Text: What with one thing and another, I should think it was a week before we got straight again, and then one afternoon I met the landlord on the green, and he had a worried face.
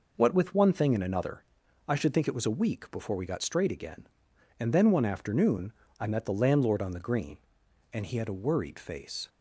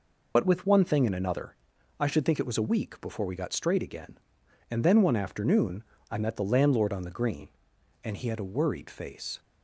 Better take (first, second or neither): first